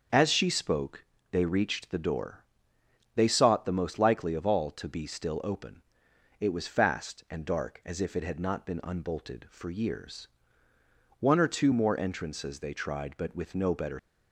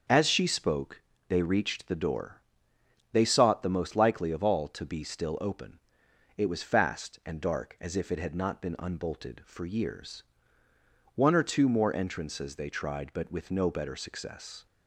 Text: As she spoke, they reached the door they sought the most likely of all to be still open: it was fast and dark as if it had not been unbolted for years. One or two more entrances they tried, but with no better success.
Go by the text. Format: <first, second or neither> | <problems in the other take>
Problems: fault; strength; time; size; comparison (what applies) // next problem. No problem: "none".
second | starts louder than the rest; until 1.4 s; 6.5 dB; also in the second // pauses between "door" and "they"; noticeable; at 2.4 s; 0.72 s long; noticeable in the second // stops before "success"; at 13.9 s